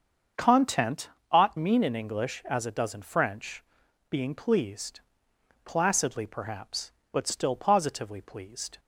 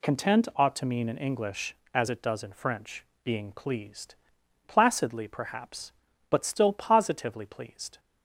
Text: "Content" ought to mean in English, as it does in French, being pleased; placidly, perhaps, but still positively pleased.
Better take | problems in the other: second | starts louder than the rest; until 1.5 s; 7 dB // pauses between "Content" and "ought"; slight; at 1.1 s; 0.20 s long // skips "to"; at 1.5 s

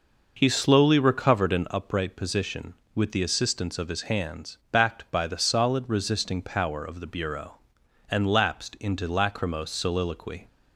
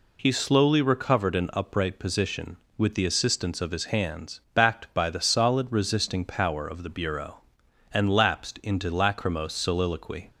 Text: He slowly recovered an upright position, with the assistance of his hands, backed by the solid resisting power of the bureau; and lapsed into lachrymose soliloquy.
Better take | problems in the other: second | starts louder than the rest; noticeable; until 1.8 s; 5.5 dB

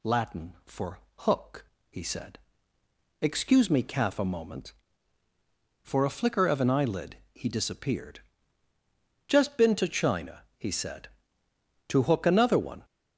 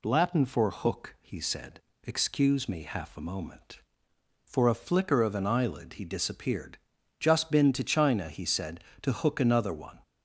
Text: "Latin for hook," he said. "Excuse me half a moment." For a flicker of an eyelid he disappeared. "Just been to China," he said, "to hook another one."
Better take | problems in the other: second | pauses between "for" and "hook"; slight; at 0.9 s; 0.22 s long // says "calf" for "half"; at 3.8 s // pauses between "eyelid" and "he"; slight; at 7.1 s; 0.16 s long

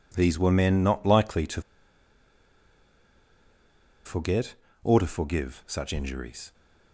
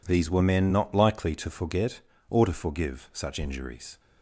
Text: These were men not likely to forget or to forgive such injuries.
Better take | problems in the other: second | pauses between "to" and "forget"; strong; at 1.6 s; 2.4 s long

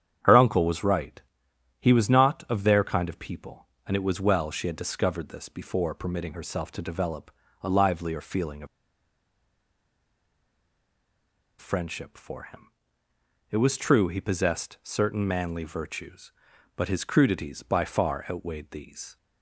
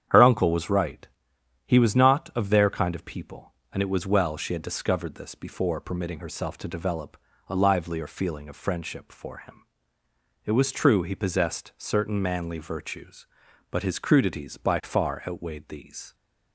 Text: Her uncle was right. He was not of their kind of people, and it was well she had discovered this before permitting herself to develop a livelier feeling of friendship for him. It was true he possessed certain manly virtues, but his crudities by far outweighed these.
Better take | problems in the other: second | starts louder than the rest; strong; until 1.8 s; 9 dB; strong in the second // pauses between "develop" and "a"; slight; at 7.3 s; 0.32 s long; slight in the second // pauses between "of" and "friendship"; strong; at 8.6 s; 2.9 s long

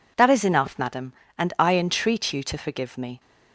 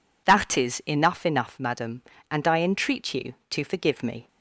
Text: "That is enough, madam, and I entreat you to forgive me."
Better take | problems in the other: first | says "enough" twice; at 1.2 s

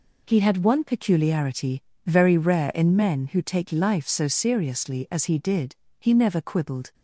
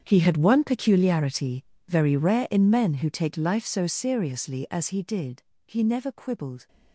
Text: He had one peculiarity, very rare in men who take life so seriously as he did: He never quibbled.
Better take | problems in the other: first | gets quieter; strong; throughout; 16.5 dB

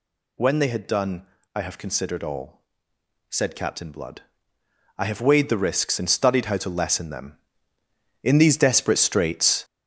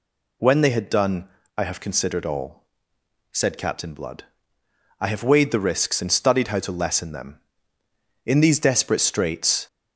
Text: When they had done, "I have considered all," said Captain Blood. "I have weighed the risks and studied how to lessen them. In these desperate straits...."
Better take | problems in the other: second | gets louder; strong; throughout; 8 dB

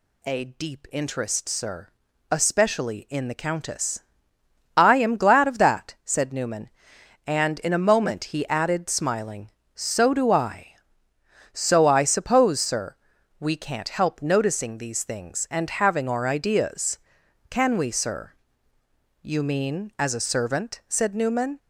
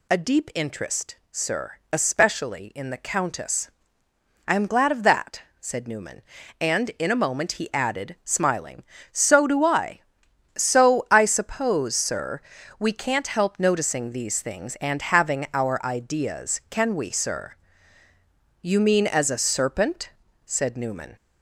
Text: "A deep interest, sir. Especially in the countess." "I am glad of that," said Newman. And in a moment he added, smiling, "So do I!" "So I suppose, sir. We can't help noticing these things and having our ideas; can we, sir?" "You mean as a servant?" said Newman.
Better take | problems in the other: first | says "serpent" for "servant"; at 19.3 s

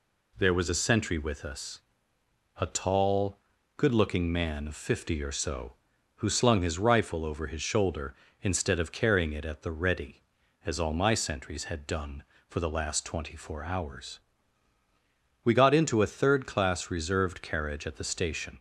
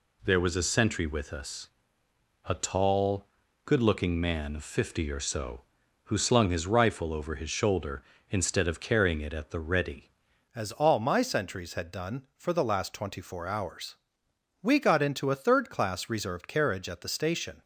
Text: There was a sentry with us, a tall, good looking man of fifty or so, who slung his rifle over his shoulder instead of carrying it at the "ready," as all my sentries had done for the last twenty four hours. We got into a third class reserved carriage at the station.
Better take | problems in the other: first | changes voice at "as"; from 10.5 s on; 7.1 s long

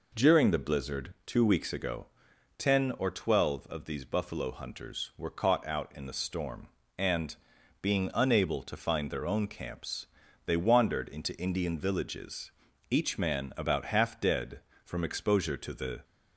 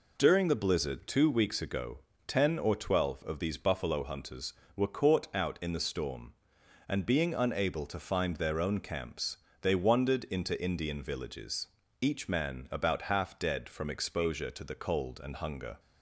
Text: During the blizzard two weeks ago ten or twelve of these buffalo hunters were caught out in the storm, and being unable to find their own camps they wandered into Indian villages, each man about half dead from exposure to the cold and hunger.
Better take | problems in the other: second | pauses between "ago" and "ten"; noticeable; at 2.0 s; 0.54 s long; slight in the second // pauses between "and" and "being"; noticeable; at 7.3 s; 0.46 s long // pauses between "camps" and "they"; at 10.0 s; 0.40 s long; slight in the second // stops before "cold and hunger"; at 16.0 s

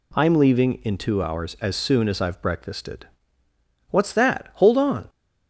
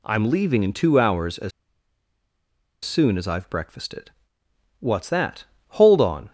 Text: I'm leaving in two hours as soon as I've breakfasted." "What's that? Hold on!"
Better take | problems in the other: first | pauses between "as" and "soon"; strong; at 1.5 s; 1.3 s long

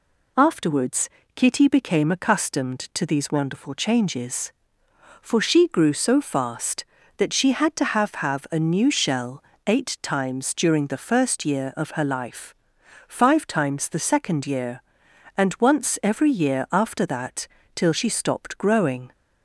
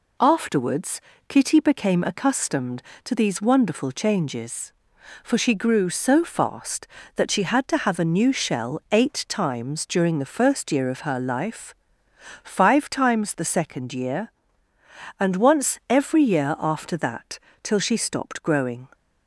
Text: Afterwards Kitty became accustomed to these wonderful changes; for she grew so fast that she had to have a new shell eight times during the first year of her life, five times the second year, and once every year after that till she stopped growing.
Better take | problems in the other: second | pauses between "Afterwards" and "Kitty"; slight; at 1.0 s; 0.26 s long; slight in the second // says "have" twice; at 8.1 s // pauses between "shell" and "eight"; slight; at 9.4 s; 0.24 s long // pauses between "that" and "till"; slight; at 17.4 s; 0.30 s long; slight in the second

